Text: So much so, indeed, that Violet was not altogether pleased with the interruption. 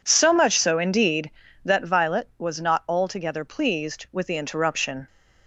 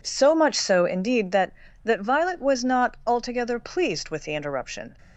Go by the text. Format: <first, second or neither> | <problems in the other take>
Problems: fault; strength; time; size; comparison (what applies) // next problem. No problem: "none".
first | says "that" twice; at 1.8 s